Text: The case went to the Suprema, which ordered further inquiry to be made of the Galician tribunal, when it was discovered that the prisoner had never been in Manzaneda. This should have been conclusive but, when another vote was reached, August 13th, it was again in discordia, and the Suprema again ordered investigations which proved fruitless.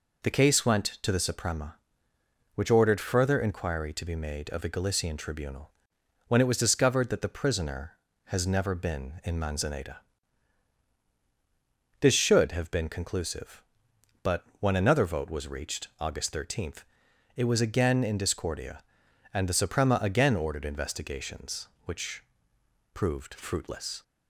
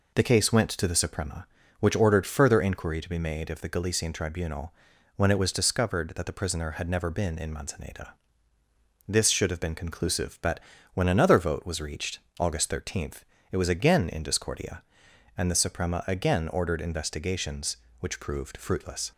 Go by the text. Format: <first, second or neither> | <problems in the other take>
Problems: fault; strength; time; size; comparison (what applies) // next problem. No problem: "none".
second | says "has" for "had"; at 8.2 s // pauses between "which" and "proved"; noticeable; at 22.2 s; 0.68 s long